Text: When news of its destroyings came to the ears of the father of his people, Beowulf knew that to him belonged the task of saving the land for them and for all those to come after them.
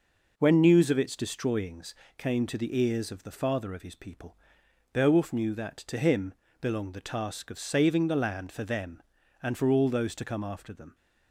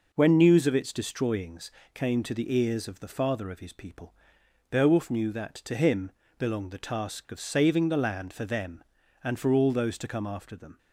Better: neither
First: pauses between "destroyings" and "came"; slight; at 1.9 s; 0.24 s long // pauses between "him" and "belonged"; slight; at 6.3 s; 0.26 s long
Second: pauses between "destroyings" and "came"; slight; at 1.6 s; 0.24 s long // pauses between "him" and "belonged"; slight; at 6.1 s; 0.26 s long

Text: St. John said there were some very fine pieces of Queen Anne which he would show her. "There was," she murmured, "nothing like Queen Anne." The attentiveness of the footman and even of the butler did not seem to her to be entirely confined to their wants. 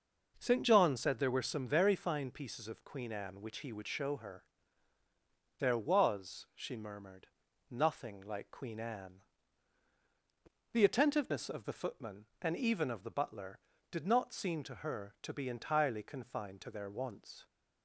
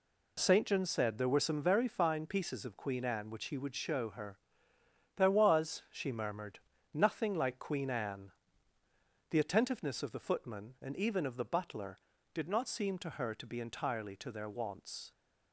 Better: first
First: none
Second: skips "confined"; at 14.1 s

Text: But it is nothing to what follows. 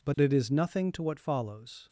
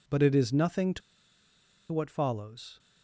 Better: first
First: none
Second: pauses between "to" and "what"; noticeable; at 1.0 s; 0.91 s long

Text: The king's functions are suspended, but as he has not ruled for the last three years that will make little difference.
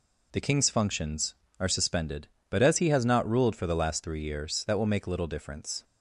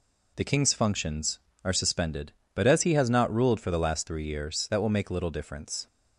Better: neither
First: none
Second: none

